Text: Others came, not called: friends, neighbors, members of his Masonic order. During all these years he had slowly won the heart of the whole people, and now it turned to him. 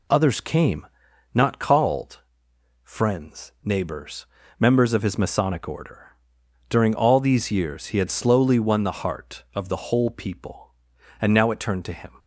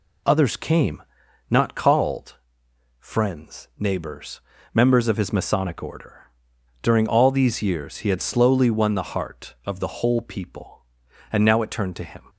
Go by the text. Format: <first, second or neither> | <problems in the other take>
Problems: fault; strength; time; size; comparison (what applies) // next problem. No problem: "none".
neither | none